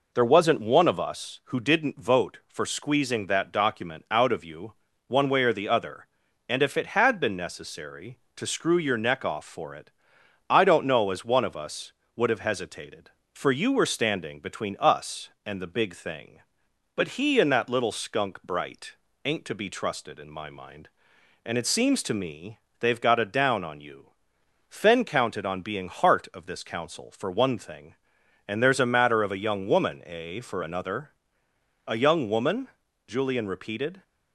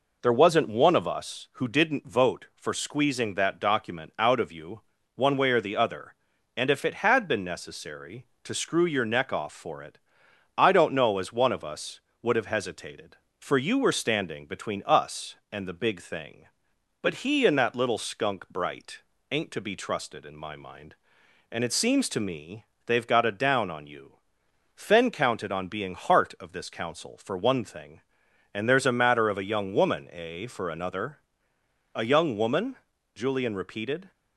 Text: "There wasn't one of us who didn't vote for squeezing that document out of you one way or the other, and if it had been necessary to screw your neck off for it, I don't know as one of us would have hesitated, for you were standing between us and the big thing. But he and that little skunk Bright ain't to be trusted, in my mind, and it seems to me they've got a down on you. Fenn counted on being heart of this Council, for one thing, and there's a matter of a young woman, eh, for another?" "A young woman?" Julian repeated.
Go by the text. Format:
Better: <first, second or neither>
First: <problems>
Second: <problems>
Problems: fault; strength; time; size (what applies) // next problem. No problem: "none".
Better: neither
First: pauses between "you" and "one"; slight; at 4.7 s; 0.34 s long // pauses between "Bright" and "ain't"; slight; at 18.9 s; 0.28 s long // pauses between "me" and "they've"; slight; at 22.5 s; 0.22 s long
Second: pauses between "you" and "one"; slight; at 4.8 s; 0.34 s long // pauses between "Bright" and "ain't"; slight; at 19.0 s; 0.28 s long // pauses between "me" and "they've"; slight; at 22.6 s; 0.22 s long